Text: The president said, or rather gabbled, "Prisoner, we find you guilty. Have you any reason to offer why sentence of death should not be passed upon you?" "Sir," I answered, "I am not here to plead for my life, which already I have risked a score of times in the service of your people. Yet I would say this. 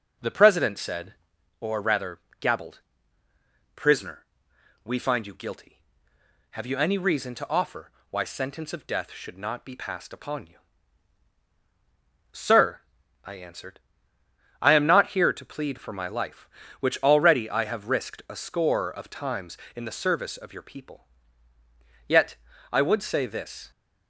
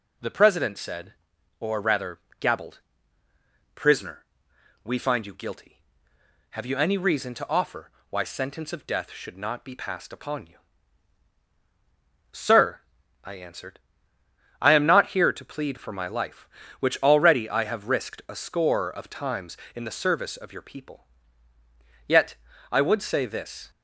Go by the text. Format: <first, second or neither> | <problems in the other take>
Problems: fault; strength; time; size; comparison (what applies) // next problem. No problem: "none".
second | starts louder than the rest; noticeable; until 1.4 s; 6 dB // pauses between "rather" and "gabbled"; slight; at 2.1 s; 0.22 s long; slight in the second // pauses between "offer" and "why"; slight; at 7.9 s; 0.18 s long; slight in the second // pauses between "Yet" and "I"; at 22.3 s; 0.38 s long; also in the second